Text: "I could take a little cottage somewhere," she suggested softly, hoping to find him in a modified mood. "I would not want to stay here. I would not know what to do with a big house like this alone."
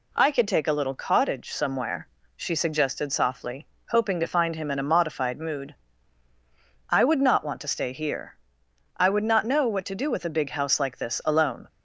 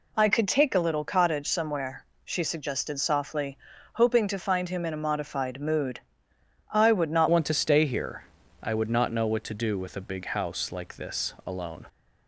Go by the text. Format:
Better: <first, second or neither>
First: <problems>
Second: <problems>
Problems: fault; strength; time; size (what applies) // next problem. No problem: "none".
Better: first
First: none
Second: changes voice at "want"; from 7.2 s on; 4.6 s long